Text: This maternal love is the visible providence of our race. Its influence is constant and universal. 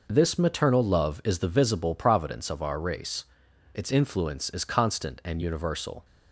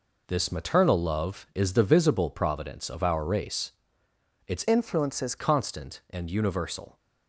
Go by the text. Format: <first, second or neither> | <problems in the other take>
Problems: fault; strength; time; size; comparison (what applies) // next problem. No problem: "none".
first | changes voice from "influence" to "is"; from 4.6 to 5.3 s; 0.7 s long